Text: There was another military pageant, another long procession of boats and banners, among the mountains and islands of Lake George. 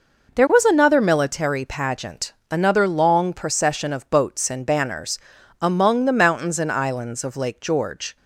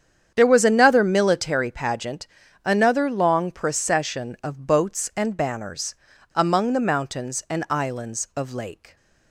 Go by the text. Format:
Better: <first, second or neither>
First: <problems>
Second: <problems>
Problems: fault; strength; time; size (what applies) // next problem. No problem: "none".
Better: first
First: none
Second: starts louder than the rest; strong; until 1.3 s; 8.5 dB // stops before "George"; at 8.9 s